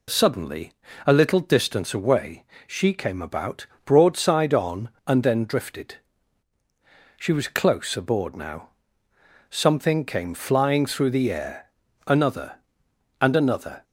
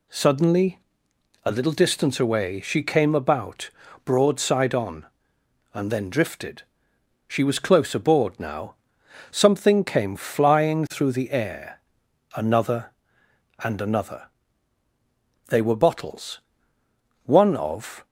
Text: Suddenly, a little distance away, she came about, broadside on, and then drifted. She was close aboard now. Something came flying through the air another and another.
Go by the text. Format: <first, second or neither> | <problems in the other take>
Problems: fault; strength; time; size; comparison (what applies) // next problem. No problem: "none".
first | pauses between "air" and "another"; noticeable; at 11.7 s; 0.56 s long; also in the first // goes on to say "They were bottles One of"; strong; from 15.4 s on; 2.5 s long